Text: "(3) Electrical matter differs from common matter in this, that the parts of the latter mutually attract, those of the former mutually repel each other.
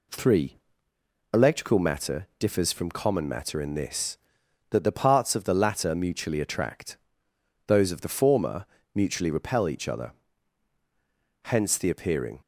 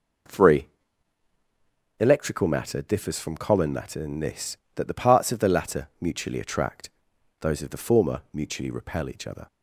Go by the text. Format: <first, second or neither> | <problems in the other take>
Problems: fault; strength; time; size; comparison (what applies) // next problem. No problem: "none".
second | pauses between "former" and "mutually"; slight; at 8.6 s; 0.30 s long // goes on to say "Hence the appearing"; noticeable; from 11.4 s on; 0.96 s long